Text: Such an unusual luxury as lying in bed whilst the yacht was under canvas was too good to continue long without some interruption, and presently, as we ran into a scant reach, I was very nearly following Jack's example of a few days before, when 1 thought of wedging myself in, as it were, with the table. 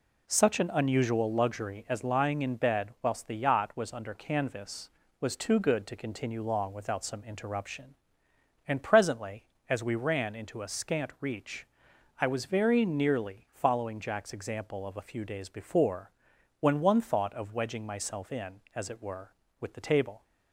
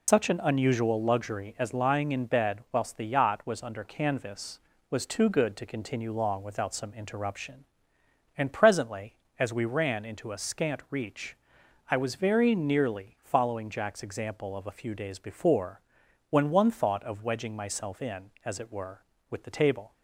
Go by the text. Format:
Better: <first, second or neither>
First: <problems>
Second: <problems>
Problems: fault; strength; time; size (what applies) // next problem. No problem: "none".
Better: first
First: none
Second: loses the start of "Such"; at 0.0 s; 110 ms